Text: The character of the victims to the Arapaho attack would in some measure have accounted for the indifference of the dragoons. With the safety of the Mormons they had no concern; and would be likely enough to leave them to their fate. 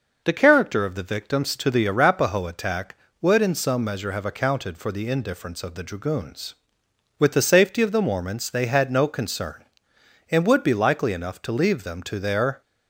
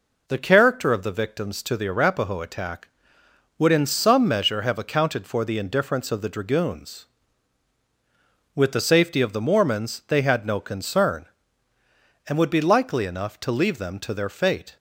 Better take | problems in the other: second | stops before "fate"; at 12.6 s

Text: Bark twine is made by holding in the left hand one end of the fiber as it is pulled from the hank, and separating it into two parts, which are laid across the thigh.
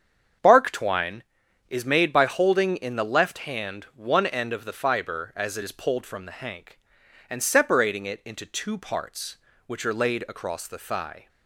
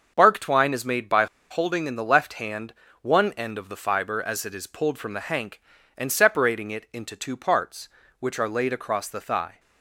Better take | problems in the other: first | starts louder than the rest; until 1.1 s; 6.5 dB; strong in the first // pauses between "by" and "holding"; slight; at 1.2 s; 0.24 s long // pauses between "hand" and "one"; slight; at 2.7 s; 0.28 s long

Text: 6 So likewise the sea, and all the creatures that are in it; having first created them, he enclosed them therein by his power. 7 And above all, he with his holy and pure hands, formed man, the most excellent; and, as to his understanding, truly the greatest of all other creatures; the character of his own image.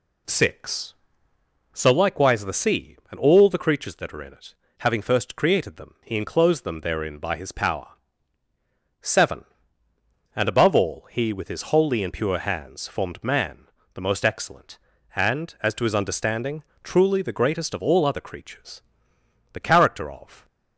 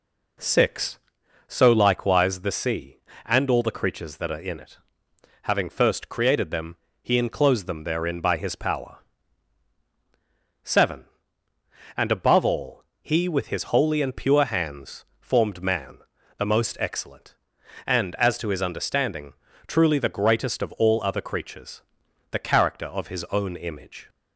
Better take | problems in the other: second | stops before "his own image"; at 20.4 s

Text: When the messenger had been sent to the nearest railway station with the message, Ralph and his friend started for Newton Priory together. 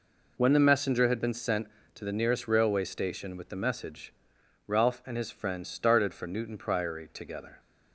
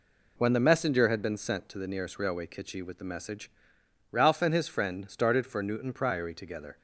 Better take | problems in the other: first | says "kitchy" for "station"; at 2.4 s

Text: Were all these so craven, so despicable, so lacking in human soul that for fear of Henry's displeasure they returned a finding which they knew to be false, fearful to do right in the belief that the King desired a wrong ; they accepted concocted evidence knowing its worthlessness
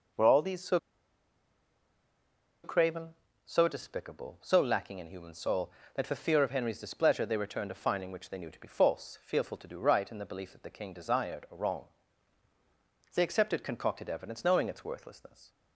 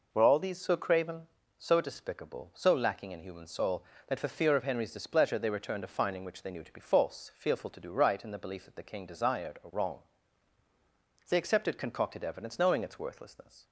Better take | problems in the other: second | pauses between "so" and "craven"; strong; at 0.7 s; 1.8 s long

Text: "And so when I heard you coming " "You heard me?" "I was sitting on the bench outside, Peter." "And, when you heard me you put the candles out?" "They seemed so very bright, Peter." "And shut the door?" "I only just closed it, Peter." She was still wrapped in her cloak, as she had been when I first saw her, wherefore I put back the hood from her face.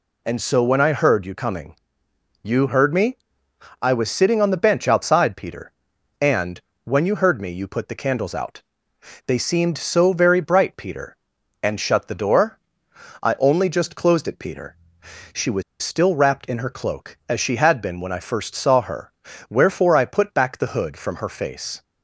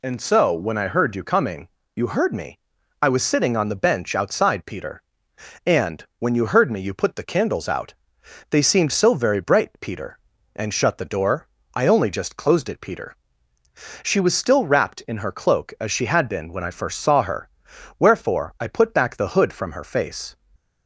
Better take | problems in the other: second | pauses between "was" and "still"; slight; at 15.6 s; 0.20 s long

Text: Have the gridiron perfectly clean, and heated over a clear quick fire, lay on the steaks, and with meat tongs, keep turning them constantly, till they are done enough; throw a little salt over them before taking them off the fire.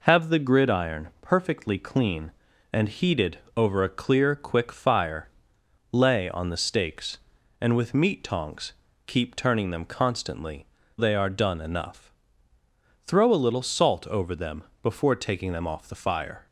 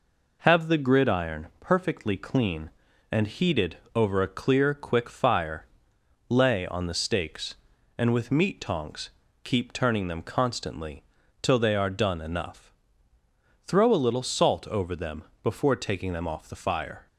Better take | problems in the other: second | pauses between "heated" and "over"; slight; at 3.3 s; 0.16 s long; slight in the second // skips "till"; at 10.8 s // pauses between "them" and "before"; slight; at 14.6 s; 0.18 s long; slight in the second

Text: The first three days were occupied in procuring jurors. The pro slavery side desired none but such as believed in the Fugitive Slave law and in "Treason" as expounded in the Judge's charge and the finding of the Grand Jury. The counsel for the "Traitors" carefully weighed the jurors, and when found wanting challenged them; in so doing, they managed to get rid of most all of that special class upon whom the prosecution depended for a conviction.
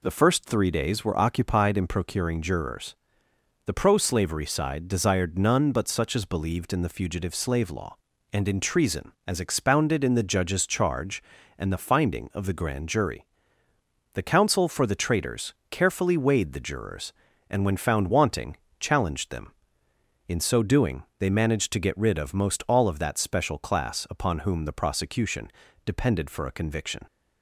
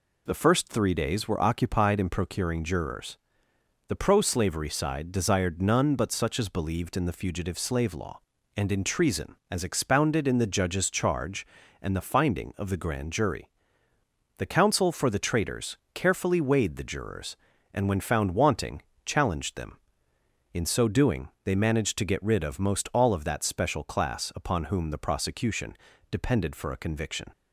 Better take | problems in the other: neither | pauses between "Traitors" and "carefully"; slight; the same in both // pauses between "wanting" and "challenged"; slight; the same in both // pauses between "prosecution" and "depended"; slight; the same in both

